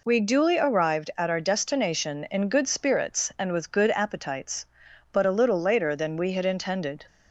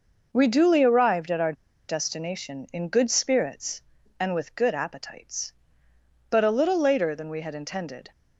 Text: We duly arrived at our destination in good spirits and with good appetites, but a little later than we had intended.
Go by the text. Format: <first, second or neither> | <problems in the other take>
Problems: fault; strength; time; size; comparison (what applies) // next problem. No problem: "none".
first | pauses between "our" and "destination"; slight; at 1.5 s; 0.35 s long